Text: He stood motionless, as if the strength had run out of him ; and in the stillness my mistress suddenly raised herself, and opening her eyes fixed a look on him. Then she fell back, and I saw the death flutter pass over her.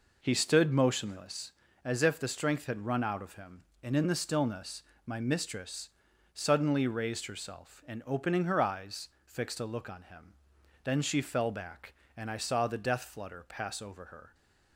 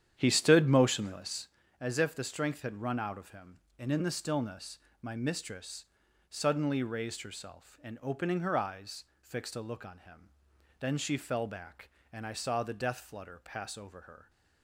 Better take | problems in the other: first | starts louder than the rest; strong; until 1.6 s; 9.5 dB // pauses between "stillness" and "my"; slight; at 4.7 s; 0.20 s long; slight in the first // pauses between "mistress" and "suddenly"; at 5.8 s; 0.44 s long; also in the first // pauses between "eyes" and "fixed"; slight; at 9.0 s; 0.16 s long; slight in the first

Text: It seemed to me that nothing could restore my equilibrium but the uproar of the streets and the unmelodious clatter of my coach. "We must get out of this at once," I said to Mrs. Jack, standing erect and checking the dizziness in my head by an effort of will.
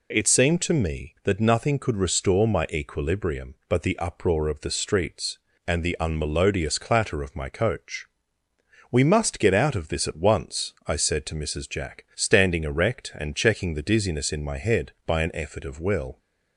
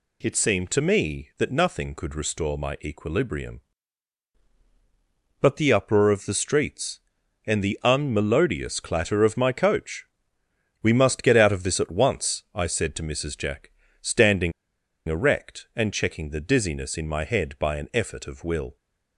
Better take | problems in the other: first | pauses between "standing" and "erect"; noticeable; at 14.5 s; 0.55 s long

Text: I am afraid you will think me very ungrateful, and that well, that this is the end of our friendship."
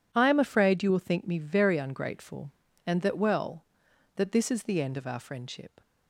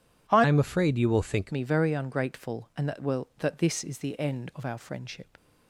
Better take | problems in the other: first | changes voice from "am" to "think"; from 0.4 to 1.5 s; 1.1 s long

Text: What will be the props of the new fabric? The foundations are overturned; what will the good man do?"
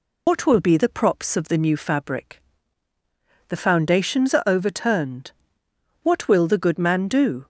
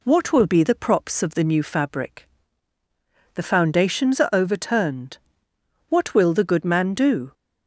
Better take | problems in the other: second | loses the start of "What"; at 0.2 s; 100 ms

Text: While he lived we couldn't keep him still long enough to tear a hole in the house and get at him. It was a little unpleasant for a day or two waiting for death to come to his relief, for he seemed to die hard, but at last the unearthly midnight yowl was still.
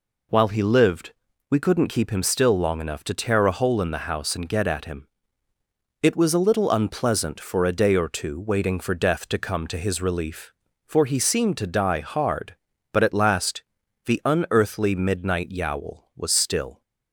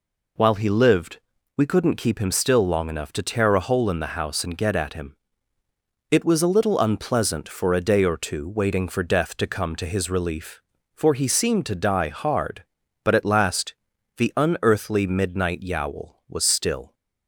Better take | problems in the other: neither | pauses between "lived" and "we"; the same in both // pauses between "last" and "the"; the same in both

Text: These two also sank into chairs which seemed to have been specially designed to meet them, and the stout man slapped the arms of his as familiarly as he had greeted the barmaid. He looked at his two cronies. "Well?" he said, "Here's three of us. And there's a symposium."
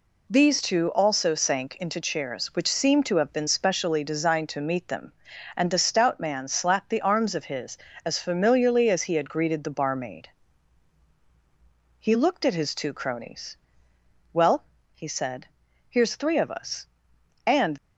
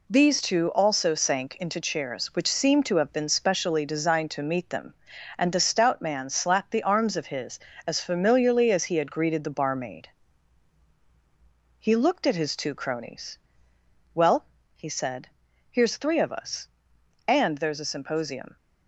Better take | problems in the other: second | stops before "there's a symposium"; at 17.7 s

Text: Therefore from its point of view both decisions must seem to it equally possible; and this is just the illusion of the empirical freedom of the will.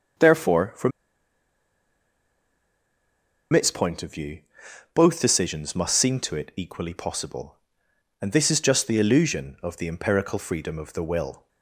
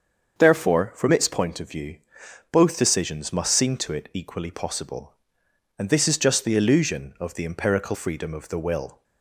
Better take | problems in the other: second | starts louder than the rest; until 3.8 s; 7 dB; also in the second // pauses between "from" and "its"; strong; at 0.9 s; 2.6 s long // pauses between "view" and "both"; noticeable; at 4.3 s; 0.54 s long; noticeable in the second

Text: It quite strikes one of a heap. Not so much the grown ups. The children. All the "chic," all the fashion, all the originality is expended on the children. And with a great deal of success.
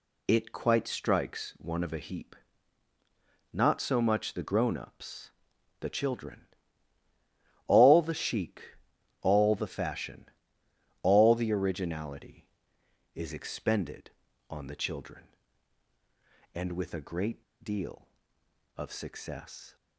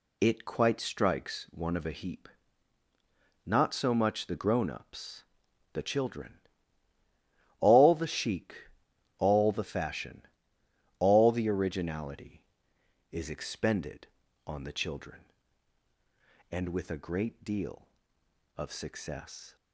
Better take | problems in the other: second | pauses between "great" and "deal"; slight; at 17.4 s; 0.19 s long

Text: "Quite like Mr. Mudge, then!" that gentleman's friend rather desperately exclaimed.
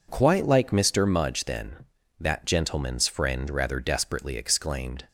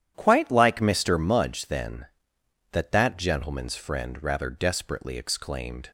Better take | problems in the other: first | starts louder than the rest; strong; until 1.1 s; 10 dB // says "that" twice; at 2.9 s

